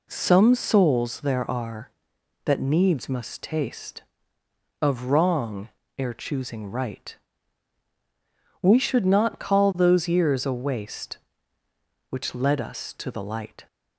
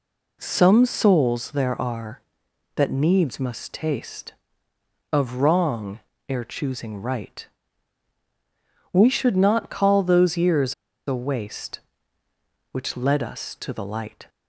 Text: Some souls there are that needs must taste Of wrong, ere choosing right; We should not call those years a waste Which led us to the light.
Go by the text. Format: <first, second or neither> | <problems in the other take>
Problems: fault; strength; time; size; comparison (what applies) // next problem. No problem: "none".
first | pauses between "years" and "a"; slight; at 10.7 s; 0.33 s long